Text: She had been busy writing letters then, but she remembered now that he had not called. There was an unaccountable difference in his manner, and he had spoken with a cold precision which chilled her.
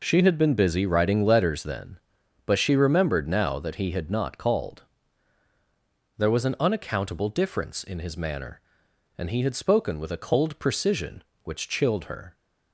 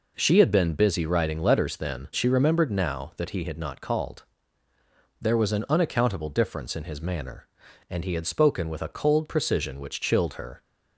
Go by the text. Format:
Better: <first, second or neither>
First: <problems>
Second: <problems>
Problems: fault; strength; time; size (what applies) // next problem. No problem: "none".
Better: first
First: none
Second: skips "but"; at 2.1 s